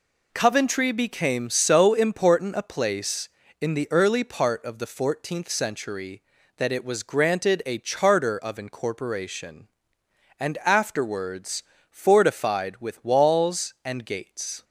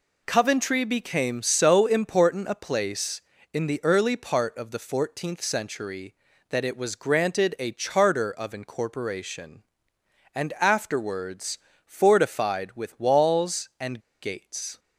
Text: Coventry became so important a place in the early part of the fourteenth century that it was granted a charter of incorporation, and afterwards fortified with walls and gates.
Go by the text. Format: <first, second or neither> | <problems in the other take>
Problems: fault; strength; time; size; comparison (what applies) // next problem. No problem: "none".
first | pauses between "afterwards" and "fortified"; slight; at 11.5 s; 0.26 s long; slight in the first // pauses between "and" and "gates"; slight; at 13.9 s; 0.23 s long